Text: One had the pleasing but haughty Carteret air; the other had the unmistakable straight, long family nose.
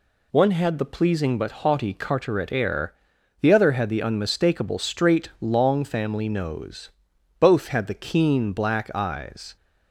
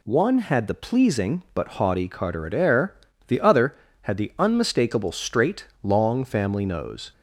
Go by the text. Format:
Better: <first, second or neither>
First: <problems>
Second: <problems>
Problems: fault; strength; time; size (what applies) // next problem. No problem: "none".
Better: second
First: goes on to say "Both had the keen black eyes"; strong; from 7.3 s on; 2.1 s long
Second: none